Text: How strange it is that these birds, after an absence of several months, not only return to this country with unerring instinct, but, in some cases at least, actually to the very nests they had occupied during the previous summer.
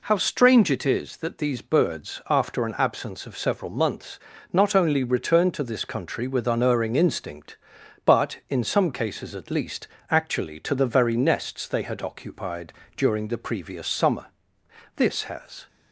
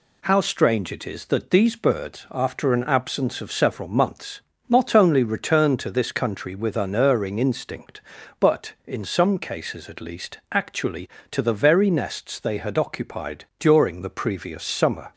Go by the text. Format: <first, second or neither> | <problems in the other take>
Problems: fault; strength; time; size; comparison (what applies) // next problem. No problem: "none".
second | pauses between "occupied" and "during"; slight; at 12.7 s; 0.24 s long // goes on to say "This has"; noticeable; from 14.9 s on; 0.72 s long